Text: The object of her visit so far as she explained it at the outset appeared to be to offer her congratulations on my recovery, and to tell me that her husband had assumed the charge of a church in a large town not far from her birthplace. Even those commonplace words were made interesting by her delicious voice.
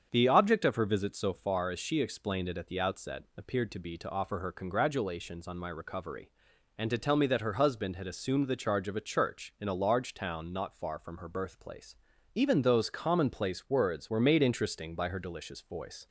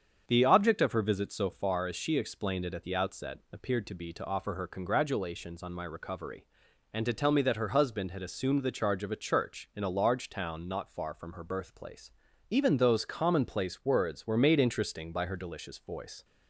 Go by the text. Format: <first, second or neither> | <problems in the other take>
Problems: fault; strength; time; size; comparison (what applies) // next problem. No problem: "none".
neither | starts louder than the rest; the same in both